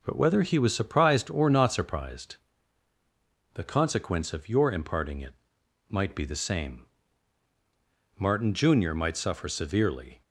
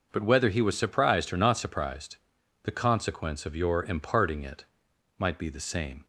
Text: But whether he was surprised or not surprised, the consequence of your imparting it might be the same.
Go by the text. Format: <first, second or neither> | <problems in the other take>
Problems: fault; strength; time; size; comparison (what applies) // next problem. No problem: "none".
second | pauses between "it" and "might"; noticeable; at 5.3 s; 0.56 s long; noticeable in the second // goes on to say "Martin junior might suffer severely"; strong; from 8.1 s on; 2.0 s long